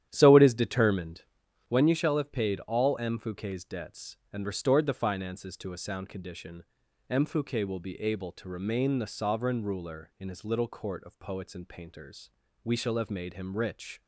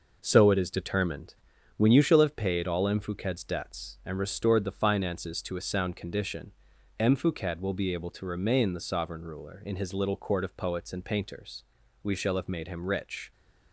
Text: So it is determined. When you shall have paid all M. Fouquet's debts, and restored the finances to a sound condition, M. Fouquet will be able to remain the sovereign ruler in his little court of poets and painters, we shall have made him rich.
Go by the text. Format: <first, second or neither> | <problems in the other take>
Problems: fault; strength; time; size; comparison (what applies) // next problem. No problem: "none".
second | starts louder than the rest; strong; until 1.6 s; 11 dB